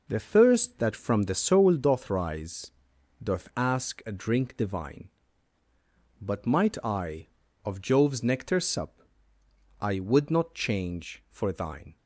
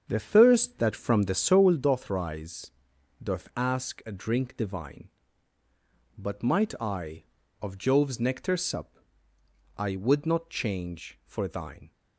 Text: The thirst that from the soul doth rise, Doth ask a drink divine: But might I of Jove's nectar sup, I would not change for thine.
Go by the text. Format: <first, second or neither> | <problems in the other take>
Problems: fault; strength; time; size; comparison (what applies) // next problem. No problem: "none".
first | starts louder than the rest; strong; until 1.8 s; 7 dB